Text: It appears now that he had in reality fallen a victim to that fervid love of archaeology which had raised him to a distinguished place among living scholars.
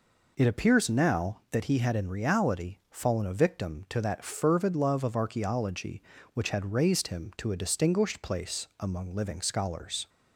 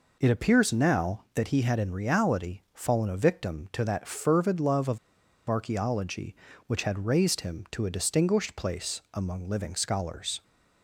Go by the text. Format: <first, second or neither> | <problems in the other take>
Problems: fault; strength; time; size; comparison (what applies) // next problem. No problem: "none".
first | pauses between "of" and "archaeology"; noticeable; at 4.9 s; 0.50 s long